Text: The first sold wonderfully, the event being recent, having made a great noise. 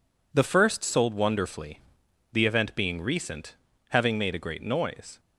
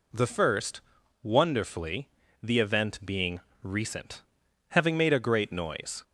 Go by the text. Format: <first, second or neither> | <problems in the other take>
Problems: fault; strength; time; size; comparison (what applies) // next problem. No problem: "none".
first | skips "sold"; at 1.0 s // pauses between "being" and "recent"; slight; at 3.3 s; 0.24 s long